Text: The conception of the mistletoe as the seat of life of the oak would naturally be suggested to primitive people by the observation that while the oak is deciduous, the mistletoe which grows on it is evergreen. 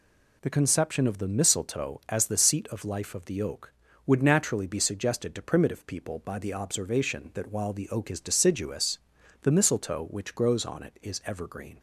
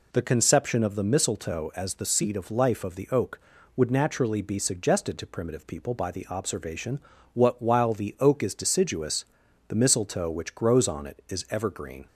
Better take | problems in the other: first | says "what" for "that"; at 7.3 s

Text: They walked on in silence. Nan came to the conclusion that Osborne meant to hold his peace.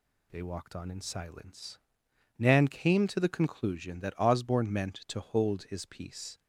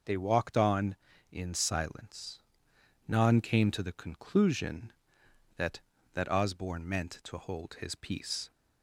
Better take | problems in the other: first | says "that" twice; at 6.1 s

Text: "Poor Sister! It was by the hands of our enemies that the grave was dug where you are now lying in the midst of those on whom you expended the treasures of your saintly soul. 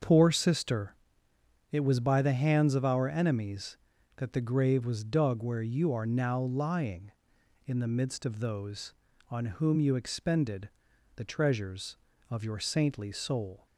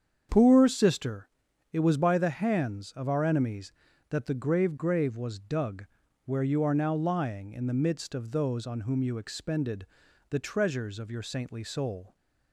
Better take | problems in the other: first | starts louder than the rest; strong; until 1.7 s; 7.5 dB; also in the first // says "grave" twice; at 4.7 s // pauses between "dug" and "where"; at 5.8 s; 0.38 s long // pauses between "expended" and "the"; at 9.8 s; 0.44 s long; noticeable in the first

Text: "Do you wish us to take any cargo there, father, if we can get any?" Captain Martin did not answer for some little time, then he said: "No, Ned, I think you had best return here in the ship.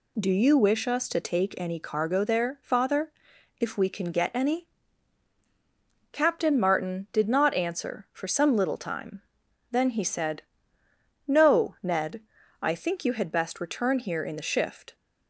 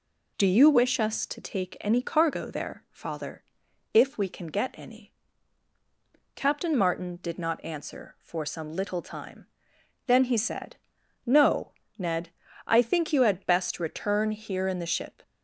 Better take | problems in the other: second | says "shift" for "ship"; at 14.4 s

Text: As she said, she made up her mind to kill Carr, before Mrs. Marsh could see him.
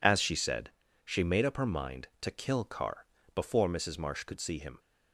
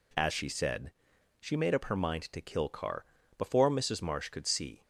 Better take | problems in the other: first | stops before "him"; at 4.8 s

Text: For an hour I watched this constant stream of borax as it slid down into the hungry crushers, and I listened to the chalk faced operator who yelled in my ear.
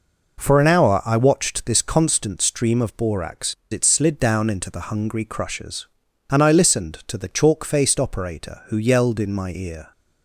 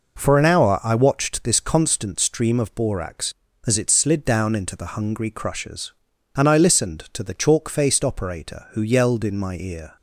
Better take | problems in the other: second | skips "as"; at 3.6 s

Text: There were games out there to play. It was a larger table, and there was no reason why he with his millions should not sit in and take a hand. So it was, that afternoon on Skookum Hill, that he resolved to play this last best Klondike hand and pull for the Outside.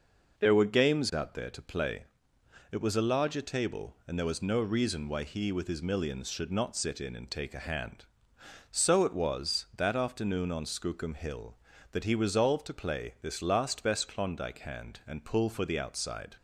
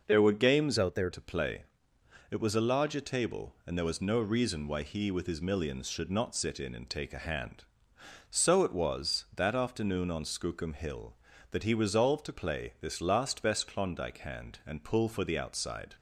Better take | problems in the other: first | changes voice from "out" to "there"; from 0.7 to 1.0 s; 0.3 s long

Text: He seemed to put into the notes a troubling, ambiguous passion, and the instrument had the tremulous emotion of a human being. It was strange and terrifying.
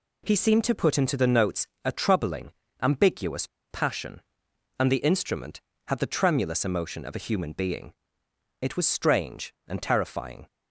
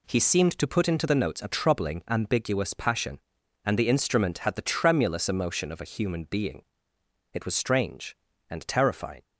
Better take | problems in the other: second | pauses between "notes" and "a"; slight; at 1.6 s; 0.18 s long // pauses between "ambiguous" and "passion"; slight; at 3.4 s; 0.24 s long

